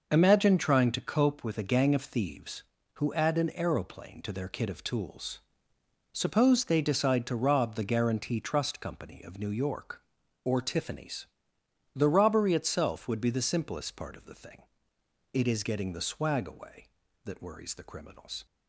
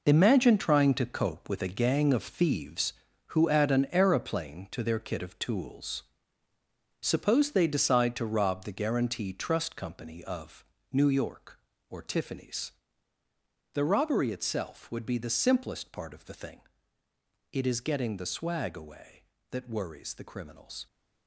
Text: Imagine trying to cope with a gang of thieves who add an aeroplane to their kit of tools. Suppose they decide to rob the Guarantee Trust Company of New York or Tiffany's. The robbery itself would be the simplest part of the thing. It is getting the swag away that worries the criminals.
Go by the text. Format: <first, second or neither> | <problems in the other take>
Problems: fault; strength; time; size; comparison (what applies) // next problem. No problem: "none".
first | gets quieter; strong; throughout; 10 dB // pauses between "of" and "New"; slight; at 10.6 s; 0.26 s long